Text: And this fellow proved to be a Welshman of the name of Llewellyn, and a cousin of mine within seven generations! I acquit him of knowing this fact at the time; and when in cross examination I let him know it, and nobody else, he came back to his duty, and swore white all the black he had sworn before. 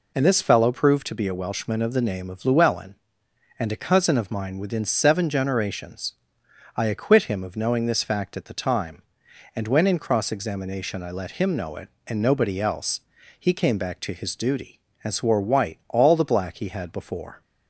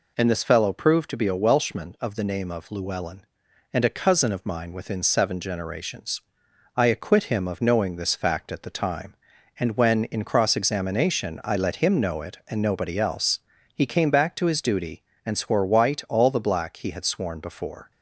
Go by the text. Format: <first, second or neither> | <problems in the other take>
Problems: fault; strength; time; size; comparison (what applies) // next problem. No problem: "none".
second | skips "sworn"; at 16.9 s